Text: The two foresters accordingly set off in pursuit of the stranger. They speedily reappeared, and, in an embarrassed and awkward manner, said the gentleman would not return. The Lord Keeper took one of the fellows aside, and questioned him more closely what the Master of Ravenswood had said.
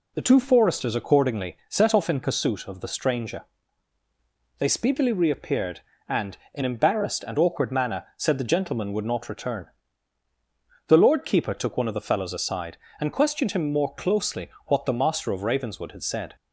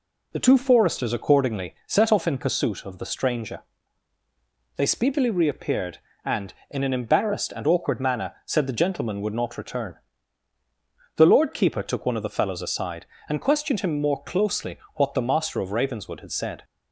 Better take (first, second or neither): second